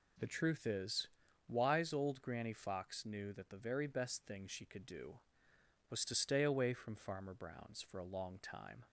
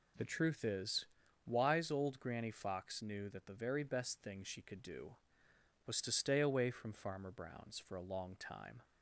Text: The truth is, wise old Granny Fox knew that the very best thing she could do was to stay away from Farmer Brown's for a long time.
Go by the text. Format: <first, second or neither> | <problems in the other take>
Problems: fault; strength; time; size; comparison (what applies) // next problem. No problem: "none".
neither | none